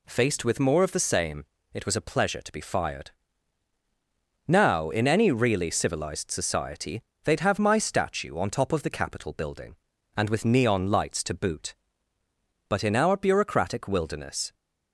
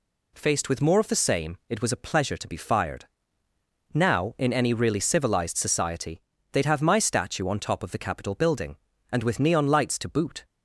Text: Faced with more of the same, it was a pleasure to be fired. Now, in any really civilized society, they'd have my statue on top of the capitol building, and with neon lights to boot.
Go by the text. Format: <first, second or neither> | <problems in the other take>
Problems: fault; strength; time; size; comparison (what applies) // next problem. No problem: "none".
second | goes on to say "But in our bureaucratic wilderness"; strong; from 12.6 s on; 1.8 s long